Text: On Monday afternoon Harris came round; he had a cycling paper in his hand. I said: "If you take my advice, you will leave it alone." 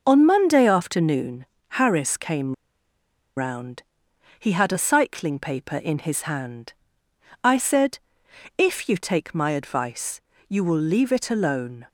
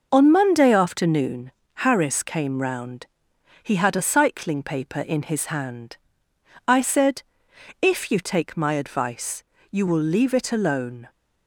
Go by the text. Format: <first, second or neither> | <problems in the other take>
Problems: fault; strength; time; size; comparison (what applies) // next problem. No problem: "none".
second | pauses between "afternoon" and "Harris"; slight; at 1.4 s; 0.32 s long; slight in the second // pauses between "came" and "round"; noticeable; at 2.5 s; 0.82 s long